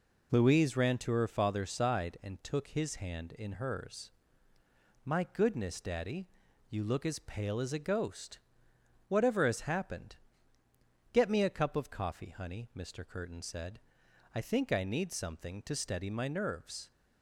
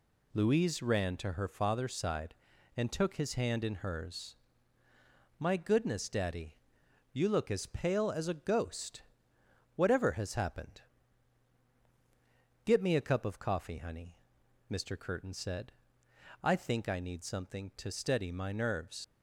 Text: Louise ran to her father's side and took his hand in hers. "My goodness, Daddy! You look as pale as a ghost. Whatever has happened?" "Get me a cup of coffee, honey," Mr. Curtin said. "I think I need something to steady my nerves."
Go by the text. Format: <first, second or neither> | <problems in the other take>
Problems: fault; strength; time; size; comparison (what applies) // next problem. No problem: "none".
first | leaves "nerves" unfinished; at 19.0 s; 70 ms